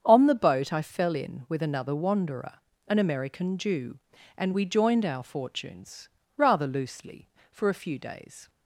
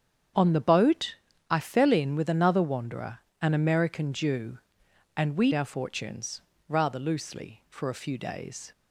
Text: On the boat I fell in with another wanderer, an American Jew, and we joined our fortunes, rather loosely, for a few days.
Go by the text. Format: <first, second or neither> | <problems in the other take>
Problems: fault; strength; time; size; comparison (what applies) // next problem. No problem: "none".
first | starts louder than the rest; strong; until 1.7 s; 8 dB; strong in the first // pauses between "boat" and "I"; slight; at 1.1 s; 0.34 s long // skips "joined"; at 5.5 s